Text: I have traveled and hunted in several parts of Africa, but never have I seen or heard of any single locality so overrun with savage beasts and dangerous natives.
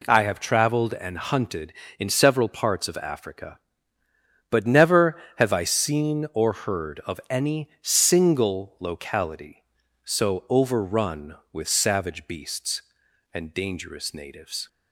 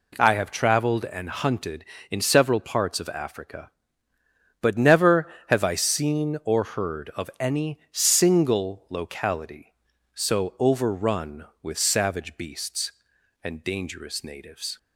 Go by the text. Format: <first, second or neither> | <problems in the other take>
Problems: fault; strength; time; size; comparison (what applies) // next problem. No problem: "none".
neither | none